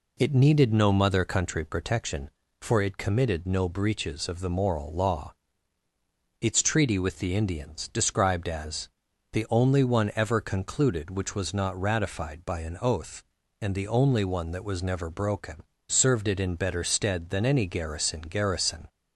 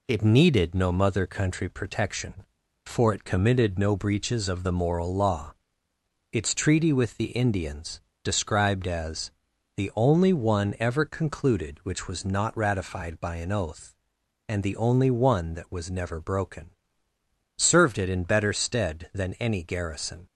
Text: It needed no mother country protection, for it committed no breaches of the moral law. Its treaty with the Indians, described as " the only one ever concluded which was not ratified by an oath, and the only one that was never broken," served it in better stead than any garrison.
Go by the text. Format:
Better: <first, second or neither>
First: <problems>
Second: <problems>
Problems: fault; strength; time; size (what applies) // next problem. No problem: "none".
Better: second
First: says "garrison" twice; at 18.2 s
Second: none